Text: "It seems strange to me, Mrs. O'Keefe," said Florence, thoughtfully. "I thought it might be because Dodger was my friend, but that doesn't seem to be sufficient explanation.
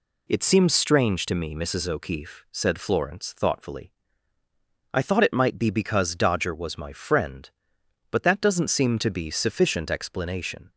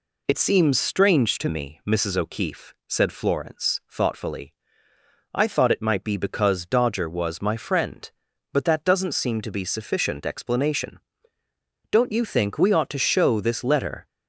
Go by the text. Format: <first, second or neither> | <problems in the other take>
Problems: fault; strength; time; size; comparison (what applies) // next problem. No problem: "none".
first | goes on to say "Don't you think we ought to show this letter"; strong; from 11.9 s on; 2.1 s long